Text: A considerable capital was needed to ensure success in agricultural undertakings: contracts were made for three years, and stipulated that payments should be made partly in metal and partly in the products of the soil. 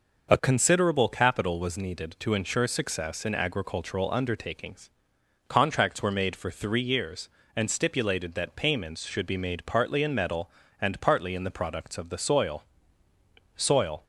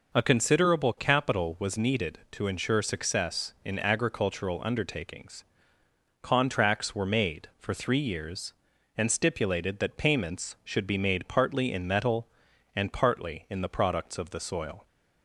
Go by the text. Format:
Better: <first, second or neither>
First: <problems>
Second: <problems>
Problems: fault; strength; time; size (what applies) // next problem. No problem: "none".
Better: second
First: says "soil" twice; at 13.5 s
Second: none